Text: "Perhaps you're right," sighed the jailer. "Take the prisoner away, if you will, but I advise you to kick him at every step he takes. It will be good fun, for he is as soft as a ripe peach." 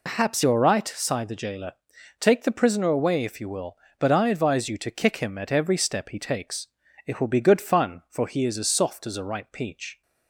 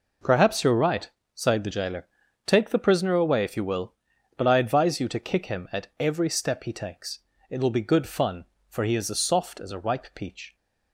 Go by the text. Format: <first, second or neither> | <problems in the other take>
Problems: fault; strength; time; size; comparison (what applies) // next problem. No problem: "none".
second | loses the start of "Perhaps"; at 0.0 s; 55 ms